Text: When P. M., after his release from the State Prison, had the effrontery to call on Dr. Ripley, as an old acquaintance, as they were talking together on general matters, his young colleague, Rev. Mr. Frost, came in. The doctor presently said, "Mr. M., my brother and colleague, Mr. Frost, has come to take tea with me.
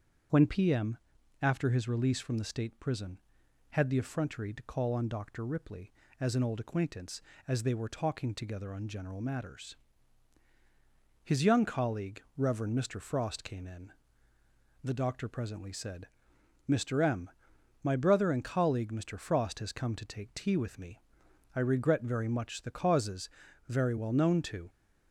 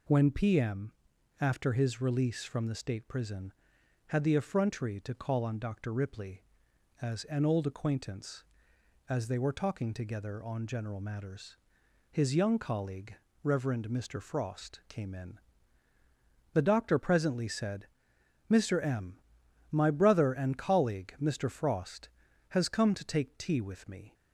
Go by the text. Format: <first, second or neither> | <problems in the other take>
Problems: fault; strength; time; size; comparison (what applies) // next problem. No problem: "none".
second | starts louder than the rest; strong; until 1.7 s; 7.5 dB // goes on to say "I regret very much the causes very well known to"; strong; from 21.5 s on; 3.1 s long